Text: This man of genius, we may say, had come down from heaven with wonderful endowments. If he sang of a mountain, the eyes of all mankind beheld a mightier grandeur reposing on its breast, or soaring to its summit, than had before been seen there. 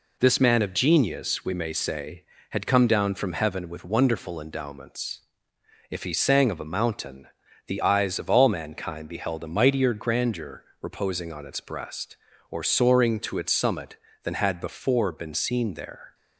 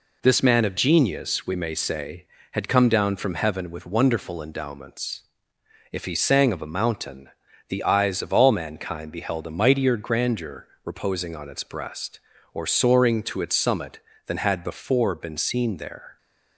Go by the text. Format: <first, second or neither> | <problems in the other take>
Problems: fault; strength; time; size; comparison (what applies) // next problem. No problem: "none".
neither | pauses between "grandeur" and "reposing"; slight; the same in both